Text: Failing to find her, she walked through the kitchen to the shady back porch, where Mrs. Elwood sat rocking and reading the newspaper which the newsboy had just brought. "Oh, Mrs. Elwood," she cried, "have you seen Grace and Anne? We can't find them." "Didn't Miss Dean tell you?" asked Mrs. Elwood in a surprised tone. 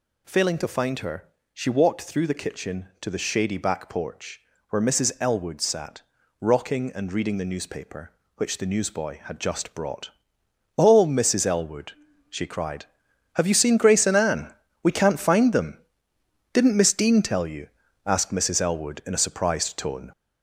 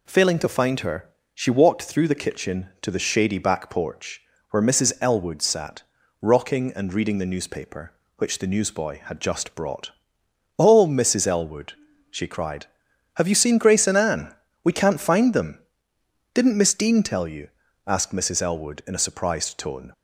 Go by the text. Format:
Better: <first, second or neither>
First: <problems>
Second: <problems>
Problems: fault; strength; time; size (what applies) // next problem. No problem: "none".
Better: second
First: gets louder; noticeable; throughout; 4.5 dB // pauses between "sat" and "rocking"; at 6.0 s; 0.40 s long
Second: pauses between "sat" and "rocking"; at 5.8 s; 0.40 s long